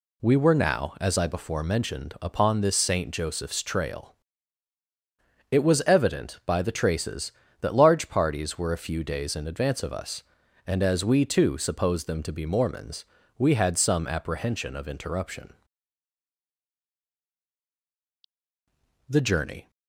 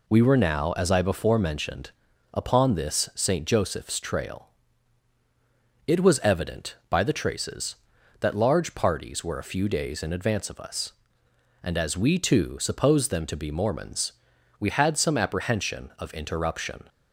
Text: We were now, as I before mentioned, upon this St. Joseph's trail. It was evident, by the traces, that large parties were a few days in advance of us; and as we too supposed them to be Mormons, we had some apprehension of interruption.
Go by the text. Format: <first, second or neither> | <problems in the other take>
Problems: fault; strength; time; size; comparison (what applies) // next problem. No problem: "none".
second | goes on to say "The journey"; noticeable; from 19.0 s on; 0.62 s long